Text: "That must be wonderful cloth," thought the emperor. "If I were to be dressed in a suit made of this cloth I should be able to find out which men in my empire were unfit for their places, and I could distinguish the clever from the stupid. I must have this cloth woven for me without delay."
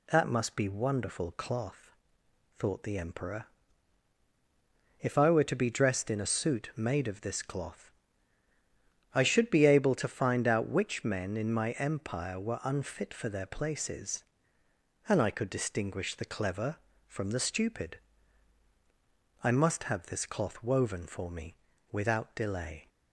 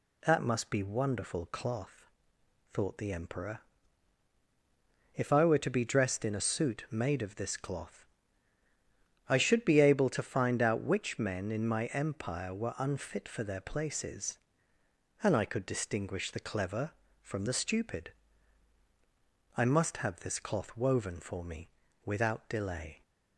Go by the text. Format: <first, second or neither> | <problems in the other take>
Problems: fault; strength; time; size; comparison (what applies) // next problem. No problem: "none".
neither | pauses between "cloth" and "I"; the same in both // pauses between "me" and "without"; the same in both